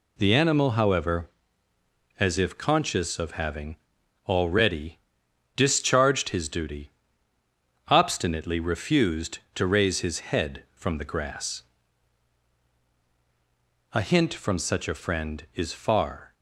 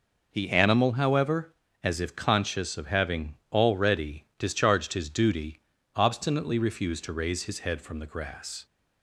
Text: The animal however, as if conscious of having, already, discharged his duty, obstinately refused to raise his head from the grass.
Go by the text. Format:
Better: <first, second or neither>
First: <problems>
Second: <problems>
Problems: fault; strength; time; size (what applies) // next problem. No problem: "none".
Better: second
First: goes on to say "A hint from such a friend is far"; strong; from 13.9 s on; 2.4 s long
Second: none